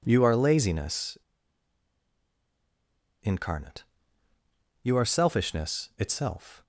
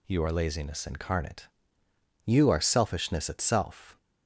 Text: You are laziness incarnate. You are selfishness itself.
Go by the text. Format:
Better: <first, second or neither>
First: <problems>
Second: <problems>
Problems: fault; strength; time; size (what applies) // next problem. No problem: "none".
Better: second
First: pauses between "laziness" and "incarnate"; strong; at 1.1 s; 2.0 s long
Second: none